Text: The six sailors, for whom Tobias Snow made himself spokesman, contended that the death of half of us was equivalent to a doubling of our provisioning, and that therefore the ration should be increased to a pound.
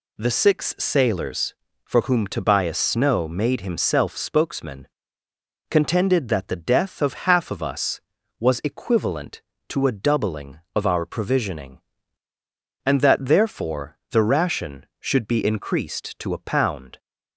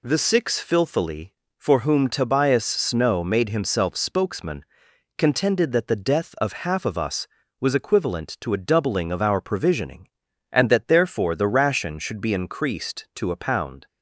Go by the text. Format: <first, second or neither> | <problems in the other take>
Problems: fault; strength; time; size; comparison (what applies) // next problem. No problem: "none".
first | says "filthily" for "sailors"; at 0.6 s